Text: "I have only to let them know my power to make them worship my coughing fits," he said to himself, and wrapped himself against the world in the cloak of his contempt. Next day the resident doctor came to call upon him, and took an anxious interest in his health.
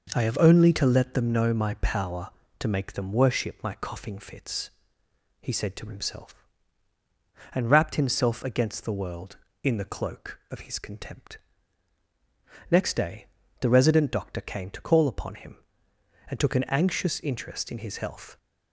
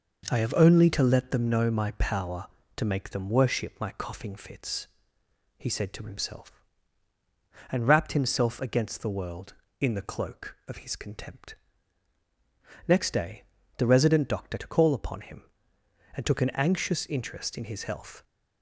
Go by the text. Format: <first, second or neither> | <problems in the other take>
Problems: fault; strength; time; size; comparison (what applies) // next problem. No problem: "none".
first | pauses between "day" and "the"; slight; at 13.4 s; 0.32 s long; slight in the first // skips "came"; at 14.5 s